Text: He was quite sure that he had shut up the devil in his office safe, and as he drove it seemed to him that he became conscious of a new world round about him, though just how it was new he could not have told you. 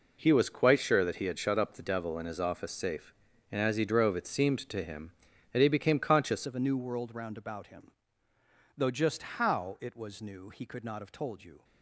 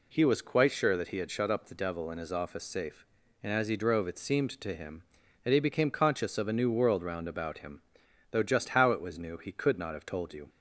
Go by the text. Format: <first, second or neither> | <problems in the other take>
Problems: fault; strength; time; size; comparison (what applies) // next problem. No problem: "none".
second | changes voice at "of"; from 6.4 s on; 5.2 s long